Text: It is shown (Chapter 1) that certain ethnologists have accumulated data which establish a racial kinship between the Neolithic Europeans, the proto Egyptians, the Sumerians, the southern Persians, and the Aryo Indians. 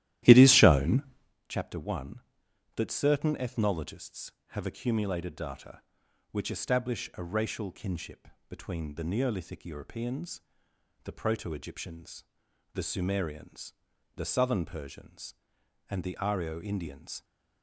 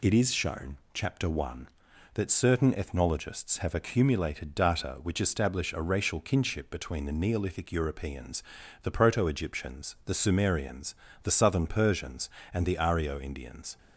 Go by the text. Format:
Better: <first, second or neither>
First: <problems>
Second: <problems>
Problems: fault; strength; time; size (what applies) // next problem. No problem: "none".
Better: second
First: starts louder than the rest; strong; until 1.4 s; 13.5 dB // pauses between "kinship" and "between"; slight; at 8.2 s; 0.20 s long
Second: none